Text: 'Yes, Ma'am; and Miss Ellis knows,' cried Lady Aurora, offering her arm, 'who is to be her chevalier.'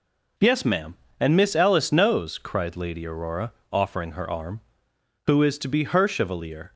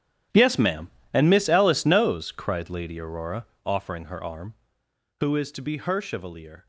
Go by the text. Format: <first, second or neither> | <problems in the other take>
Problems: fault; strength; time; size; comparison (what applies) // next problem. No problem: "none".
first | gets quieter; strong; throughout; 16 dB